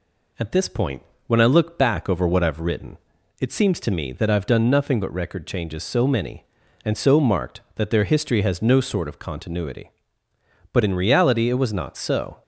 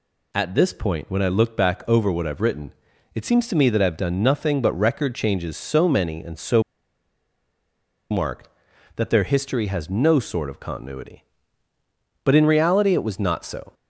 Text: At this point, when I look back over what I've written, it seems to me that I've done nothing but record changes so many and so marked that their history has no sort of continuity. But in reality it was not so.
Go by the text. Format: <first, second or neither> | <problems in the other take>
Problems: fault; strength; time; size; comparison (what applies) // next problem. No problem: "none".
first | pauses between "so" and "marked"; strong; at 6.6 s; 1.4 s long